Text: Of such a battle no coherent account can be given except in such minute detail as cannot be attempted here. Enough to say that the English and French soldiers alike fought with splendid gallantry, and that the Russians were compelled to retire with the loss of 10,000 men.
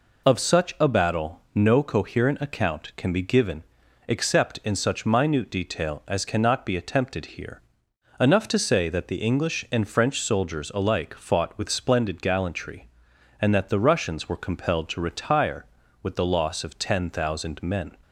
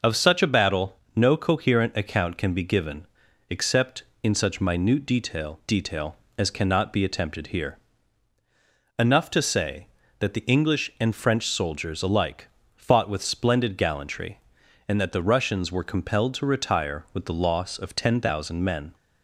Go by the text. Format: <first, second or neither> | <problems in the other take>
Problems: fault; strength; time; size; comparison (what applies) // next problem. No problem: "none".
first | pauses between "battle" and "no"; slight; at 0.9 s; 0.16 s long // pauses between "given" and "except"; at 3.0 s; 0.42 s long; noticeable in the first // says "detail" twice; at 5.6 s // pauses between "alike" and "fought"; slight; at 12.4 s; 0.26 s long